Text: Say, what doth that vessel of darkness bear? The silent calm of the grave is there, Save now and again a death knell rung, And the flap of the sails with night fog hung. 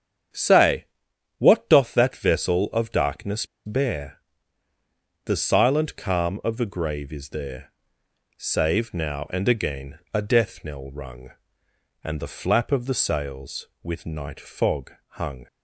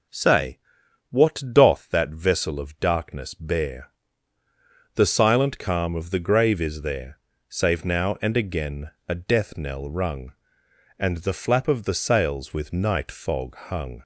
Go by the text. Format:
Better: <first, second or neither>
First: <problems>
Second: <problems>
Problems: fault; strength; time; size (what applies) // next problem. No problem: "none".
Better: second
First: starts louder than the rest; strong; until 1.8 s; 8.5 dB // pauses between "darkness" and "bear"; slight; at 3.4 s; 0.21 s long // pauses between "again" and "a"; slight; at 9.9 s; 0.16 s long // pauses between "fog" and "hung"; slight; at 14.9 s; 0.18 s long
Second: starts louder than the rest; until 1.7 s; 7 dB // pauses between "again" and "a"; slight; at 8.9 s; 0.16 s long